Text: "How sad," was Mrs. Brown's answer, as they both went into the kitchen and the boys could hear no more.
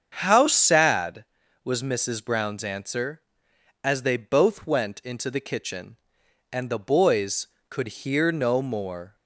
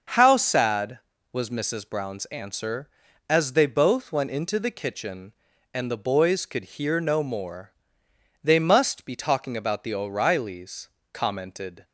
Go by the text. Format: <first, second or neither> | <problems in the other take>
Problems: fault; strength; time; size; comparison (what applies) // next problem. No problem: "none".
first | starts louder than the rest; until 1.4 s; 6.5 dB; strong in the first // goes on to say "They must be talking about the O'Reillys commented"; strong; from 8.4 s on; 3.4 s long